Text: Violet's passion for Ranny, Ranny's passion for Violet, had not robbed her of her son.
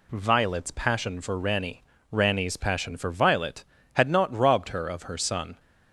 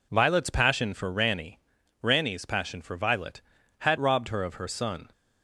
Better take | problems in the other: first | skips "not"; at 3.9 s

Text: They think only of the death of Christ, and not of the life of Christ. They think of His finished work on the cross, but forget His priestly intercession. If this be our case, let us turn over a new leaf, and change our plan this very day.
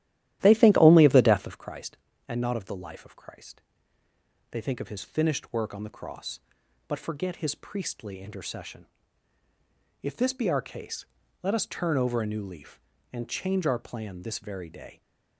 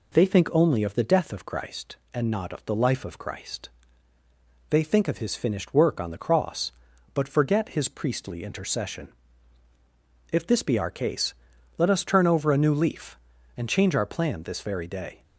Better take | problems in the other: second | starts louder than the rest; strong; until 1.7 s; 13.5 dB

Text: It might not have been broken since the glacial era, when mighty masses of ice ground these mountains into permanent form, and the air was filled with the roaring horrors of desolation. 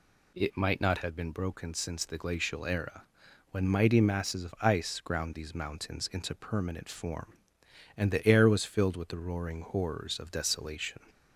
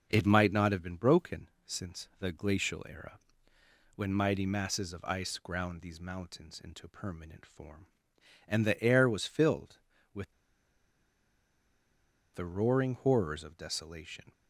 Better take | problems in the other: first | pauses between "broken" and "since"; slight; at 1.4 s; 0.16 s long // pauses between "with" and "the"; strong; at 10.3 s; 2.0 s long

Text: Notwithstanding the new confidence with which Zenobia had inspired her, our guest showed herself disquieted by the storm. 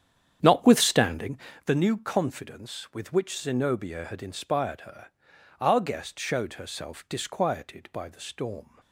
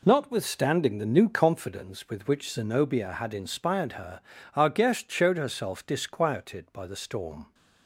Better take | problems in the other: second | starts louder than the rest; strong; until 1.4 s; 9 dB // pauses between "Notwithstanding" and "the"; slight; at 1.3 s; 0.28 s long

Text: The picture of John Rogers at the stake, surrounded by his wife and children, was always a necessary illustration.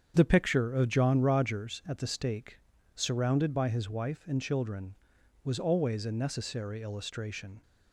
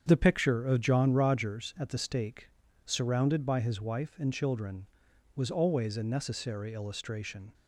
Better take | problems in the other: neither | starts louder than the rest; strong; the same in both

